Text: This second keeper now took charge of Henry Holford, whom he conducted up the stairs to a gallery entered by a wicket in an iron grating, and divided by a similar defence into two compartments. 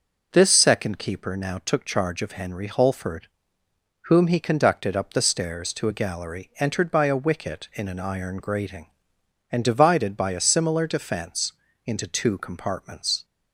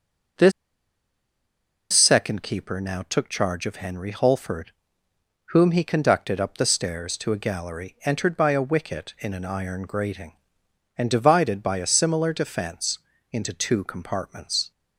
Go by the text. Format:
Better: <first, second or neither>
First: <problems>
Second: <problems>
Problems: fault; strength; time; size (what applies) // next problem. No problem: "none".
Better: first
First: pauses between "defence" and "into"; slight; at 11.5 s; 0.34 s long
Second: pauses between "This" and "second"; strong; at 0.5 s; 1.4 s long // pauses between "defence" and "into"; slight; at 12.9 s; 0.34 s long